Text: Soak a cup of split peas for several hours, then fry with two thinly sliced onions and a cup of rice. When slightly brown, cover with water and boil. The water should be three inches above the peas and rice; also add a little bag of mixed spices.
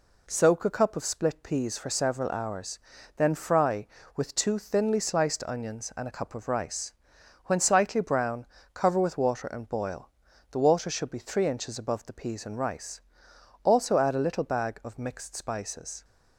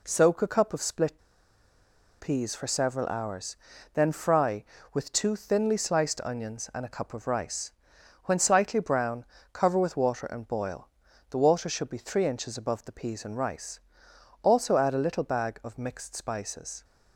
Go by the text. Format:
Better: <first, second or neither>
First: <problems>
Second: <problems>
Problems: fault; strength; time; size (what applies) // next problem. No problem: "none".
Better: first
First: none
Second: pauses between "split" and "peas"; at 1.1 s; 1.0 s long